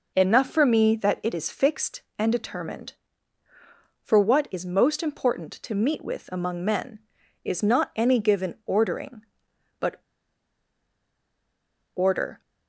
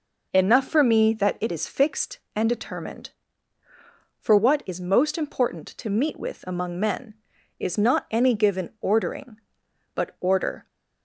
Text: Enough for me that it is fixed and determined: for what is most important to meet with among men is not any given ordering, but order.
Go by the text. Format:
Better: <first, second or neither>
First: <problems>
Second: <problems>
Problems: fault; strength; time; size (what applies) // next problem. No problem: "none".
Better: second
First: pauses between "but" and "order"; strong; at 10.0 s; 1.9 s long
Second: none